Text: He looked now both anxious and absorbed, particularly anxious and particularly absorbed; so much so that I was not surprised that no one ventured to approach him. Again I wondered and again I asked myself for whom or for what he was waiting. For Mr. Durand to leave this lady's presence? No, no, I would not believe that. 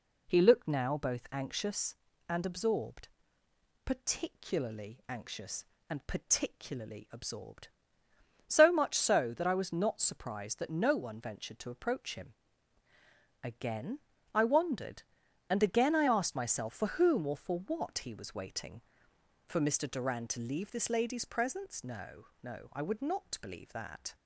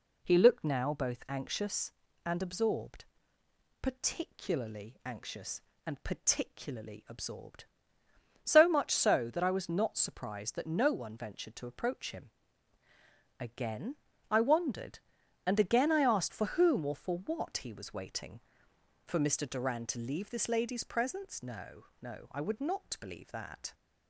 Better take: first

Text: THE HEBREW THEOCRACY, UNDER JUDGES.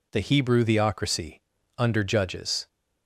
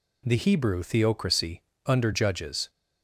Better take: neither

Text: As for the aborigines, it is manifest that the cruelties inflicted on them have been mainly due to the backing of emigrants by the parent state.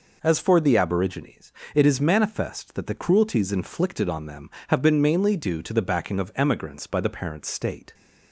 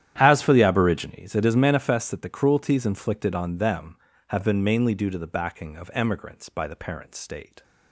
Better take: first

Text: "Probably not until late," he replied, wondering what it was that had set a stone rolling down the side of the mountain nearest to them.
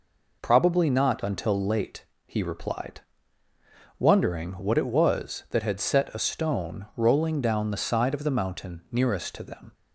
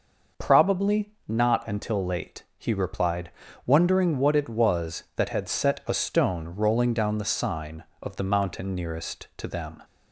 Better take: first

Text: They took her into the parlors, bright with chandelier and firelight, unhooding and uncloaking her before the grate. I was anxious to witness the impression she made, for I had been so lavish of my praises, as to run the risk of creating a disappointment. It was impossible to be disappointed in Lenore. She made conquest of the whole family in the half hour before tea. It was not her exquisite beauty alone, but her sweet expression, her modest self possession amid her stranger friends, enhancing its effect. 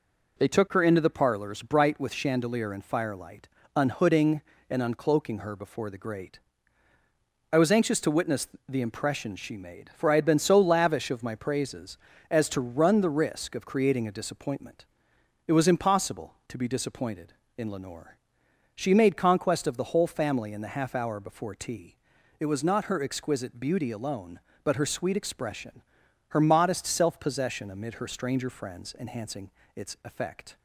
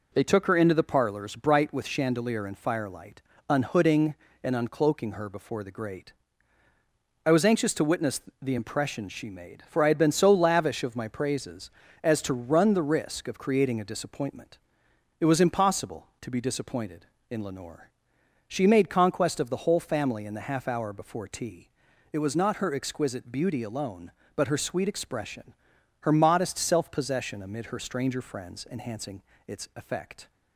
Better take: neither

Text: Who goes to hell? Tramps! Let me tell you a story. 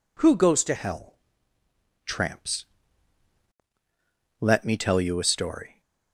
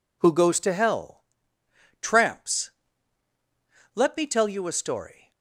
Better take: second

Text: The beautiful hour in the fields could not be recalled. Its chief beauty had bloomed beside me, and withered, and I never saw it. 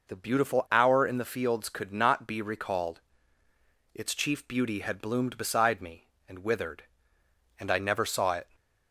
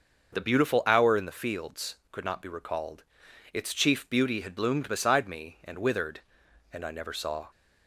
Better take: first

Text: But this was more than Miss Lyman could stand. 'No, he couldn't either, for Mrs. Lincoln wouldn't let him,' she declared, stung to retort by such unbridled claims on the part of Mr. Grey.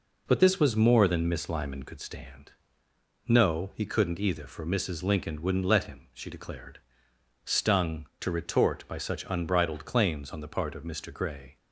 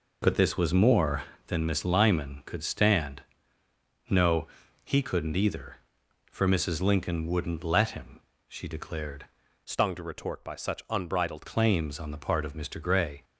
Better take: first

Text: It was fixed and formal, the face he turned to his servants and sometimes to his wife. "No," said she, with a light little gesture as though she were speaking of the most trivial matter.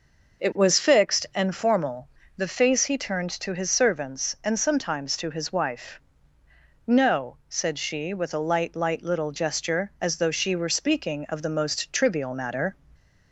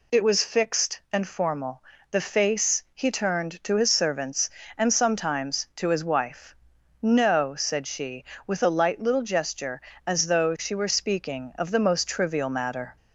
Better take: second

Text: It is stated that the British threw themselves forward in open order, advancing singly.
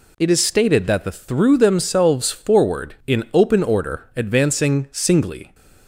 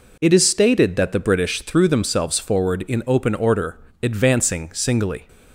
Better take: second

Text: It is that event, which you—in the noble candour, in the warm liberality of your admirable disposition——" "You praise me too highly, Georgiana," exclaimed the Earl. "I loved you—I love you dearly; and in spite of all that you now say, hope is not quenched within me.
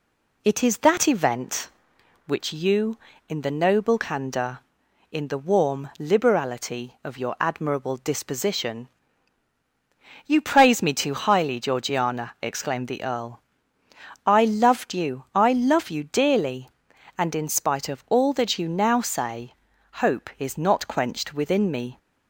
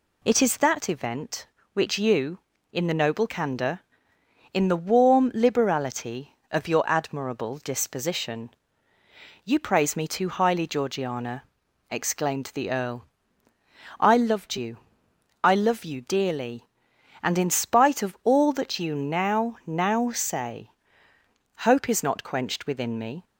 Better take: first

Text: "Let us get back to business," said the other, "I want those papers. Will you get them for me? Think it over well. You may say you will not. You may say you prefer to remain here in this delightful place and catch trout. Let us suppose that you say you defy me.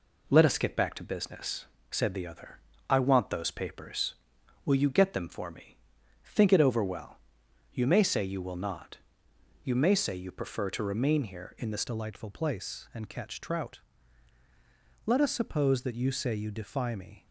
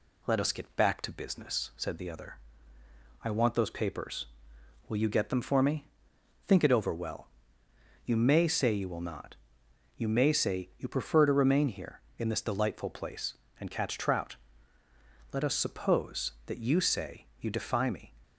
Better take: second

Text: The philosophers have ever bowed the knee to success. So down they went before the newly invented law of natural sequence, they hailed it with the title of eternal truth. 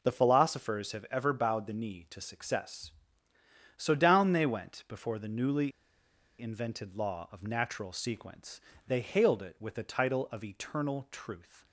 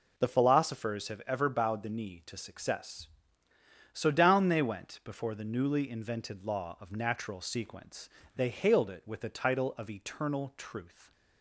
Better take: second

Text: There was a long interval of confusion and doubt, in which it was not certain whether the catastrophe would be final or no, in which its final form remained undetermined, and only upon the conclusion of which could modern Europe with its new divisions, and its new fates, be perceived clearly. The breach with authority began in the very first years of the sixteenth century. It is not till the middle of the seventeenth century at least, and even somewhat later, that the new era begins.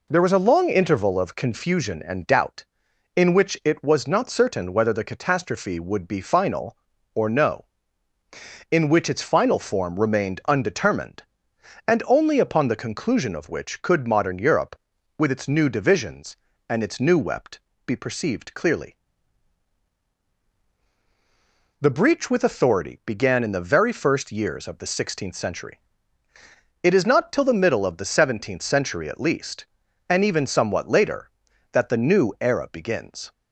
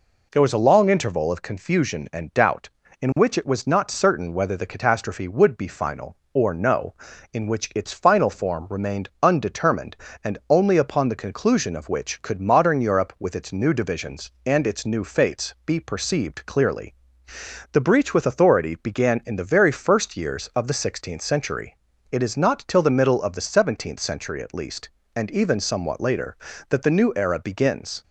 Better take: second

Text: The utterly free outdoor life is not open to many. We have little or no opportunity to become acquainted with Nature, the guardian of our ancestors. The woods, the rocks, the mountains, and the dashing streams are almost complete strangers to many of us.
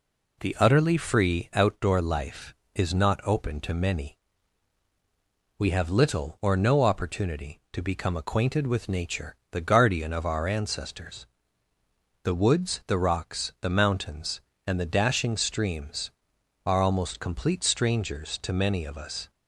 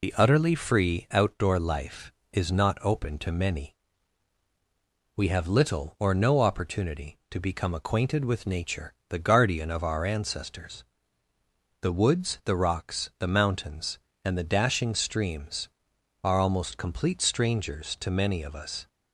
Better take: first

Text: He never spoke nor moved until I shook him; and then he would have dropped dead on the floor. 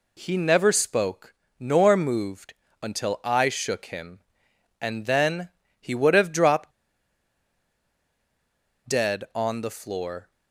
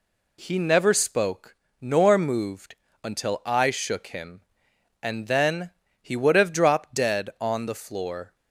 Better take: second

